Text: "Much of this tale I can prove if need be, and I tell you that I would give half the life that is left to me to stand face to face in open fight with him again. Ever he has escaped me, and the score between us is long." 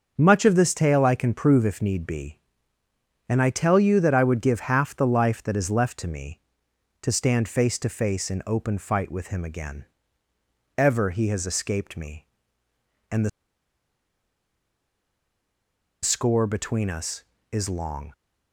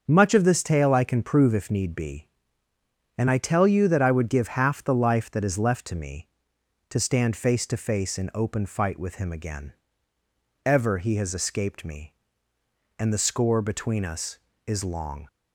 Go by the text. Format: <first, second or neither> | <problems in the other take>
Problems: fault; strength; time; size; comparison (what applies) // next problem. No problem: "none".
second | starts louder than the rest; until 1.1 s; 6.5 dB; also in the second // pauses between "the" and "score"; strong; at 13.2 s; 2.7 s long